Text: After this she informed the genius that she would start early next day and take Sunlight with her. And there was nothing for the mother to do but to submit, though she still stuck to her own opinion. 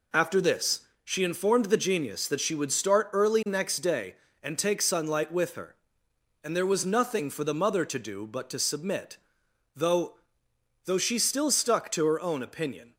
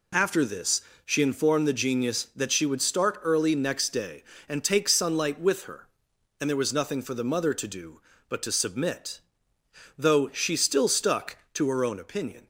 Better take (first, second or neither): second